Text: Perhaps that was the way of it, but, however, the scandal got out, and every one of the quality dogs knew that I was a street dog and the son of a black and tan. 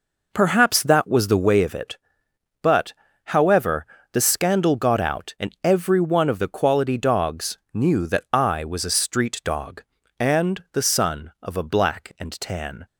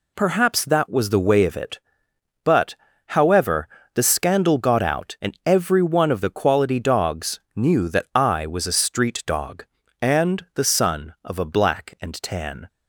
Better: second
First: starts louder than the rest; noticeable; until 1.5 s; 5 dB // pauses between "dogs" and "knew"; slight; at 7.5 s; 0.16 s long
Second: pauses between "dogs" and "knew"; slight; at 7.3 s; 0.16 s long

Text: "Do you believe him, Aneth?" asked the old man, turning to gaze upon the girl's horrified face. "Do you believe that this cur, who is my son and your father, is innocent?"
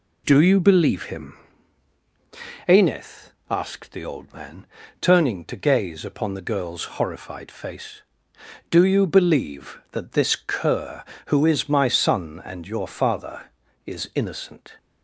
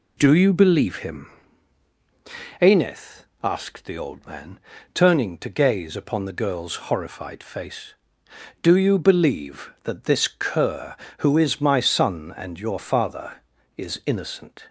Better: neither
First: none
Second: none

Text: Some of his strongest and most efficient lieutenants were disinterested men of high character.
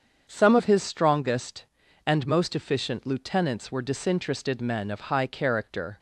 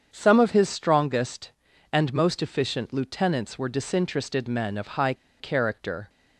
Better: first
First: starts louder than the rest; until 1.3 s; 7 dB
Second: starts louder than the rest; strong; until 1.1 s; 7 dB // pauses between "high" and "character"; slight; at 5.1 s; 0.26 s long

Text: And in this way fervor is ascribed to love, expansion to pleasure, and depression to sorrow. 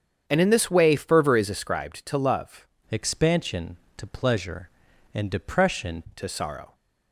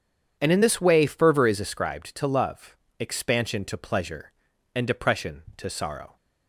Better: second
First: starts louder than the rest; strong; until 1.2 s; 7.5 dB // changes voice from "expansion" to "depression"; from 2.9 to 6.0 s; 3.1 s long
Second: none

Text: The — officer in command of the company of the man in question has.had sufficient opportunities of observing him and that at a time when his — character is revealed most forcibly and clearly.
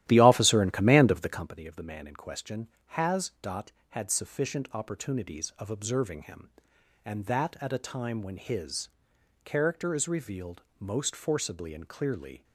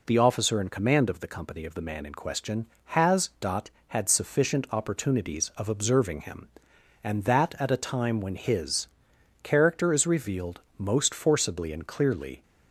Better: second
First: starts louder than the rest; strong; until 1.5 s; 13 dB // pauses between "revealed" and "most"; slight; at 10.6 s; 0.16 s long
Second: pauses between "revealed" and "most"; slight; at 10.6 s; 0.16 s long

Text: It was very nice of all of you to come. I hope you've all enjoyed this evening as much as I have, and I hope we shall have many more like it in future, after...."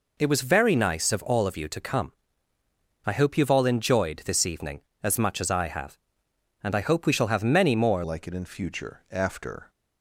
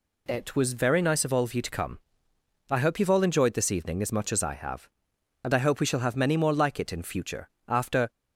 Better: second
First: changes voice at "like"; from 8.0 s on; 1.6 s long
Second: none

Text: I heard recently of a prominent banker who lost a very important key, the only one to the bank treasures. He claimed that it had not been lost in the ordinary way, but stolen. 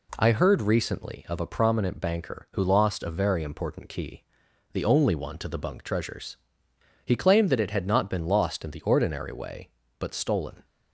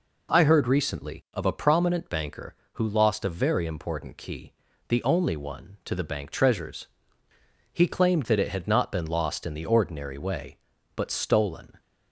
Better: second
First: says "bunk" for "bank"; at 5.5 s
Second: none

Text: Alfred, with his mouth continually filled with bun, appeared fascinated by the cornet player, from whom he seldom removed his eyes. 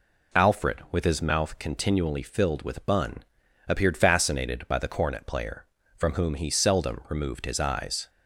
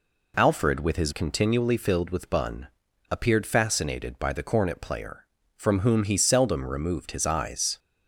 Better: first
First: none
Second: skips "mouth"; at 1.1 s

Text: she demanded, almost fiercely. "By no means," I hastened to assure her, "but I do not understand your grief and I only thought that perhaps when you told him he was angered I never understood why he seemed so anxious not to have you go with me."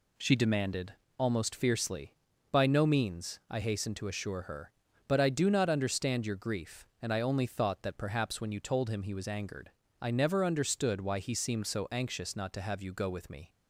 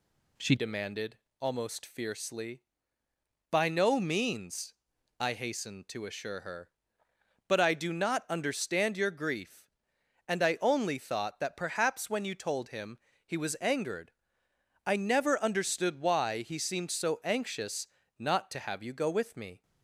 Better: first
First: pauses between "angered" and "I"; slight; at 9.7 s; 0.28 s long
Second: changes voice at "demanded"; from 0.5 s on; 19.1 s long // pauses between "him" and "he"; slight; at 12.9 s; 0.26 s long // pauses between "angered" and "I"; noticeable; at 14.1 s; 0.74 s long // pauses between "anxious" and "not"; slight; at 17.8 s; 0.32 s long

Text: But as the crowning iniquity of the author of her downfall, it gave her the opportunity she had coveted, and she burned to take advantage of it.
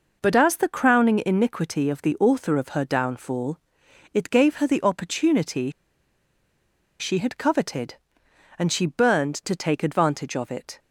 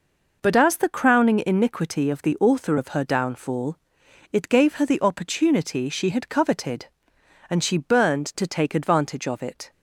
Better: second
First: pauses between "opportunity" and "she"; strong; at 5.6 s; 1.3 s long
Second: none

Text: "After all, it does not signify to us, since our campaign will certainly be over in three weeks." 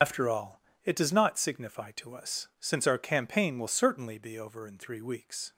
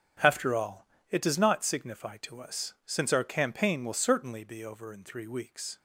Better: second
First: loses the start of "After"; at 0.0 s; 95 ms // starts louder than the rest; strong; until 1.2 s; 7.5 dB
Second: starts louder than the rest; strong; until 1.4 s; 7.5 dB

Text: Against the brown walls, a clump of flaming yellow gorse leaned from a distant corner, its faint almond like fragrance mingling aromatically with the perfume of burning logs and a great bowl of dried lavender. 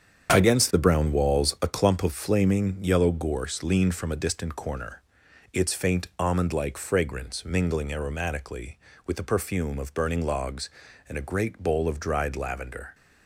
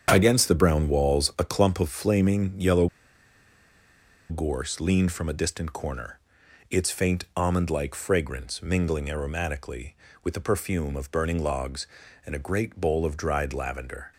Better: first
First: starts louder than the rest; strong; until 1.3 s; 7.5 dB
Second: starts louder than the rest; strong; until 1.1 s; 8 dB // pauses between "yellow" and "gorse"; strong; at 2.8 s; 1.4 s long

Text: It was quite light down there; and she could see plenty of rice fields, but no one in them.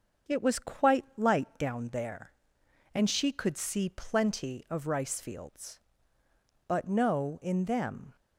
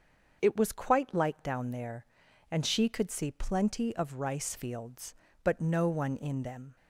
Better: second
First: starts louder than the rest; until 1.4 s; 6.5 dB // skips "one"; at 7.4 s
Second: starts louder than the rest; until 1.4 s; 6.5 dB

